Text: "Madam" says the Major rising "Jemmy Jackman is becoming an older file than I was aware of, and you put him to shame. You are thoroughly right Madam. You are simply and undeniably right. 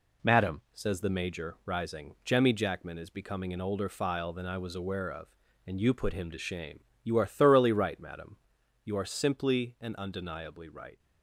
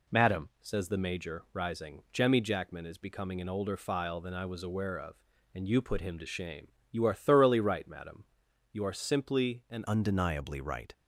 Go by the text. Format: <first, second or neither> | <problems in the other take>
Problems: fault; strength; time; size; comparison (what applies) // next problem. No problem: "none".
first | changes voice at "undeniably"; from 9.8 s on; 1.1 s long